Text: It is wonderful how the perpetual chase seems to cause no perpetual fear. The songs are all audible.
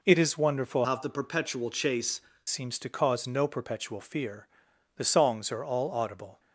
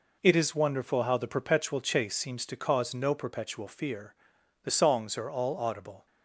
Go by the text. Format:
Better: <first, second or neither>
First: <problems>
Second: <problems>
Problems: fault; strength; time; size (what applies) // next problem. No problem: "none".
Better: second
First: changes voice from "how" to "chase"; from 0.8 to 2.1 s; 1.3 s long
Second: none